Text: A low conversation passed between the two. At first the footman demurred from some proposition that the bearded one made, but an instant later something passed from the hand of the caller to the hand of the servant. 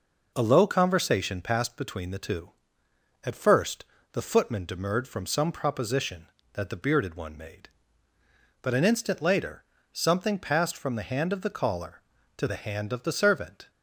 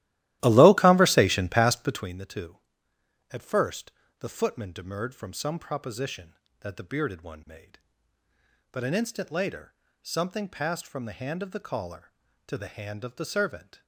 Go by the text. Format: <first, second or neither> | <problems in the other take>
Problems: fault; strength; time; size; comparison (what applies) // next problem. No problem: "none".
first | starts louder than the rest; strong; until 2.2 s; 15 dB // pauses between "first" and "the"; slight; at 3.9 s; 0.28 s long; slight in the first // pauses between "later" and "something"; slight; at 9.7 s; 0.28 s long; slight in the first